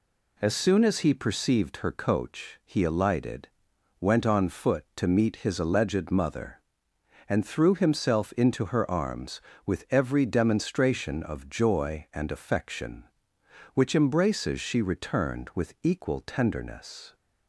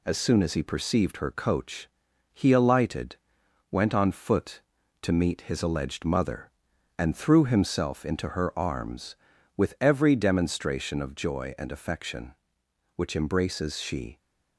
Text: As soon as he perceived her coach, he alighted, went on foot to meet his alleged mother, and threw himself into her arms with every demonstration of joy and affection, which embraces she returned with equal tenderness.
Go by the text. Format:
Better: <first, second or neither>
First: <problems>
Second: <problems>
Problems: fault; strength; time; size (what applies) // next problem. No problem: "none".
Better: first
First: none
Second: stops before "returned with equal tenderness"; at 14.1 s